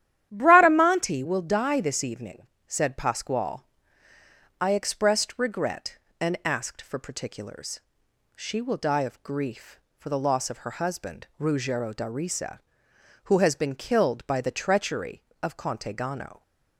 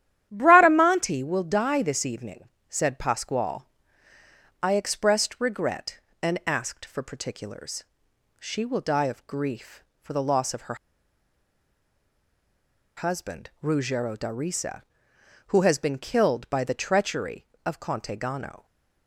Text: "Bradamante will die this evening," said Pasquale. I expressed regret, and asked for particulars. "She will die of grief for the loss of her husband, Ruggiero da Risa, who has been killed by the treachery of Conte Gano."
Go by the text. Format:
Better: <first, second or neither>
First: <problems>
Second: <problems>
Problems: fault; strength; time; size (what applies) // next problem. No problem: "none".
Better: first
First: starts louder than the rest; strong; until 1.3 s; 11.5 dB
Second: starts louder than the rest; strong; until 1.3 s; 11.5 dB // pauses between "her" and "husband"; strong; at 10.7 s; 2.2 s long